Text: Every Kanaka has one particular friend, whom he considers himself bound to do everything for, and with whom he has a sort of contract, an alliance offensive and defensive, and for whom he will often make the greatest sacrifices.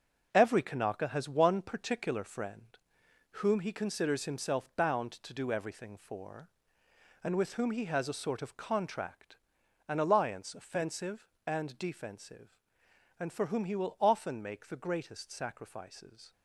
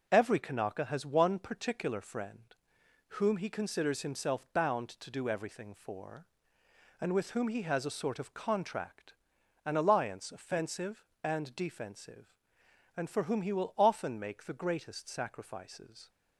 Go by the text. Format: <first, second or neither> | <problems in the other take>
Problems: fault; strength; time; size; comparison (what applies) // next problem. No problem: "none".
second | gets quieter; strong; throughout; 7.5 dB